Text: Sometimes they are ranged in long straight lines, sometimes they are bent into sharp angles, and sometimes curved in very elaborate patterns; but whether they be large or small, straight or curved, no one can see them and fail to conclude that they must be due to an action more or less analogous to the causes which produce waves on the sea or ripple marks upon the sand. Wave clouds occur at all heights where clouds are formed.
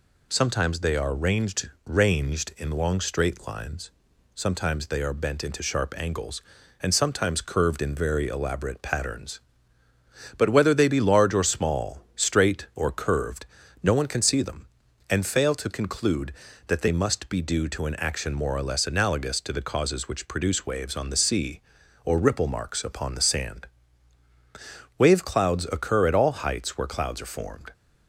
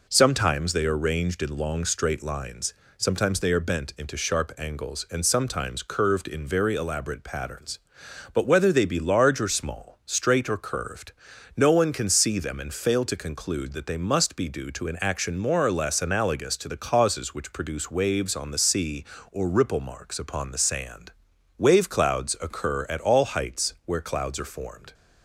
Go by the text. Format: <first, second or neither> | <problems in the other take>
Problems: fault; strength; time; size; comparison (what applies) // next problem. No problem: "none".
second | says "ranged" twice; at 1.8 s